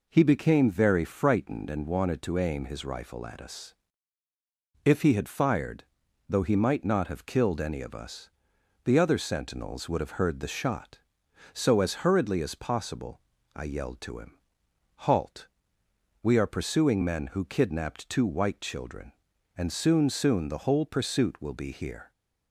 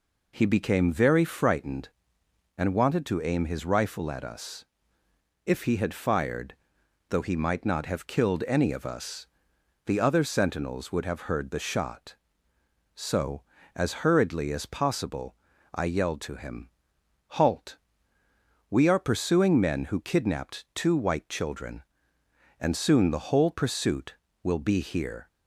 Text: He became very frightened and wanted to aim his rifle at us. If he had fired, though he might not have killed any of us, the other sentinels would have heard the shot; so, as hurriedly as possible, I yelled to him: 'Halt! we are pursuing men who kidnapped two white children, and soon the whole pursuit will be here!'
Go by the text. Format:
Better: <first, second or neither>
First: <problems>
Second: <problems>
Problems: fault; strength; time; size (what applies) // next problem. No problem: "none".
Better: second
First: says "soon" twice; at 20.1 s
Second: none